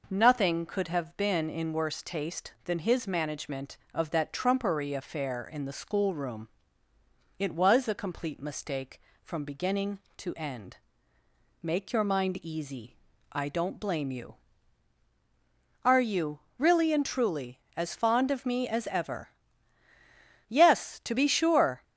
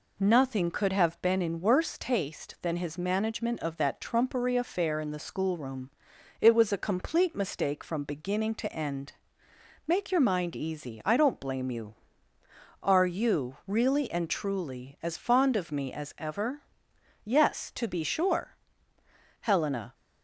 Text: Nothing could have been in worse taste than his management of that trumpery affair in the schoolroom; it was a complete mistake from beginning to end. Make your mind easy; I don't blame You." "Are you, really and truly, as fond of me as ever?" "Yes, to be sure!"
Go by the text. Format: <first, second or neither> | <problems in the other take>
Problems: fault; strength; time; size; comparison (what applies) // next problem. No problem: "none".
first | goes on to say "Helena"; from 19.4 s on; 0.52 s long